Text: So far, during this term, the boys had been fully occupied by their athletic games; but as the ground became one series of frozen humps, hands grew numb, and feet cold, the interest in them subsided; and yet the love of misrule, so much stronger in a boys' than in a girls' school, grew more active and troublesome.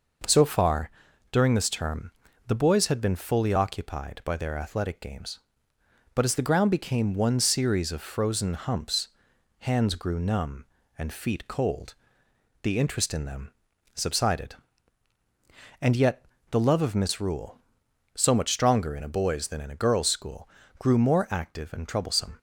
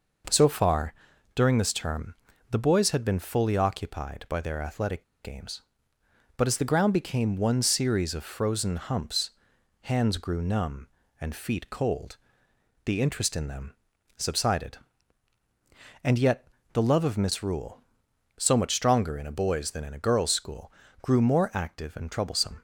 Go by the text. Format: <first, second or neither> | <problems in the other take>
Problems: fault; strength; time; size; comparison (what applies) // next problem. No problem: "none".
first | pauses between "athletic" and "games"; slight; at 5.0 s; 0.18 s long // pauses between "them" and "subsided"; noticeable; at 13.7 s; 0.46 s long; noticeable in the first // pauses between "yet" and "the"; slight; at 16.4 s; 0.28 s long; slight in the first